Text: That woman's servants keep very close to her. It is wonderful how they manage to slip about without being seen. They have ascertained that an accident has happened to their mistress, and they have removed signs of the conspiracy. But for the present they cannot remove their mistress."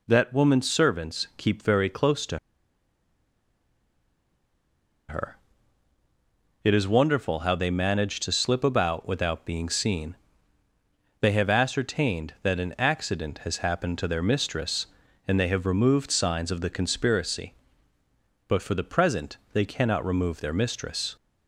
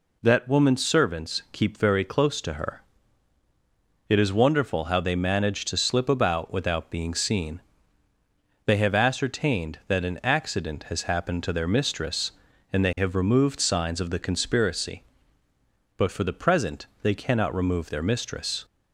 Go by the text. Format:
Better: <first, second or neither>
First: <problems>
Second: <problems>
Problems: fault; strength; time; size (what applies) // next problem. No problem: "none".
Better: second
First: pauses between "to" and "her"; strong; at 2.3 s; 2.7 s long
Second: none